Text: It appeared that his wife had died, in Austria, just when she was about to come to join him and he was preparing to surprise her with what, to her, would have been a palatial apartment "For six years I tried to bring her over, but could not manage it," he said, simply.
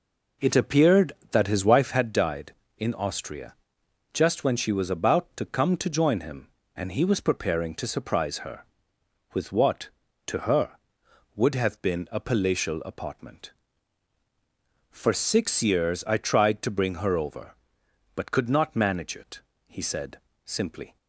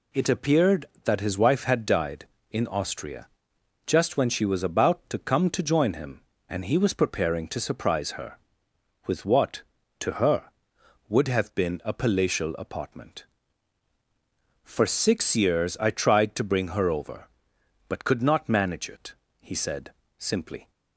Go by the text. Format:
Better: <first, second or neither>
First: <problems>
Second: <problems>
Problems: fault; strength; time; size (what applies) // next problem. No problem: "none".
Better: second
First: starts louder than the rest; noticeable; until 2.1 s; 4.5 dB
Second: none